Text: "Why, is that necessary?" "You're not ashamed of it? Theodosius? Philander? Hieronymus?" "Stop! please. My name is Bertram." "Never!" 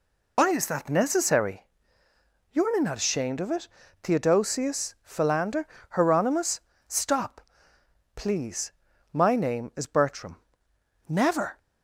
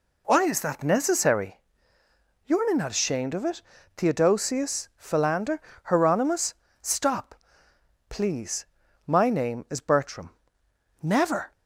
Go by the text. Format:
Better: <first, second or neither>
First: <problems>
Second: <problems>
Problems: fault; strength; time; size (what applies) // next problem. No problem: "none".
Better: second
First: loses the start of "Why"; at 0.3 s; 60 ms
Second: none